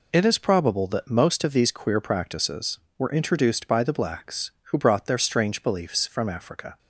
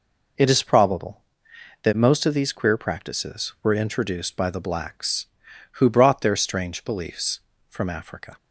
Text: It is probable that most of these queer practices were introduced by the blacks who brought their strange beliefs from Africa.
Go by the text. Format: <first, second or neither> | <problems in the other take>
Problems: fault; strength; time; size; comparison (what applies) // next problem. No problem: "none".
neither | none